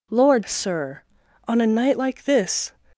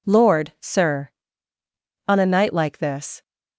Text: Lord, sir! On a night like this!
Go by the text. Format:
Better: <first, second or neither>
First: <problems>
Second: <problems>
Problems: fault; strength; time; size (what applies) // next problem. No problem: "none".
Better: second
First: changes voice at "sir"; from 0.4 s on; 2.3 s long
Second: none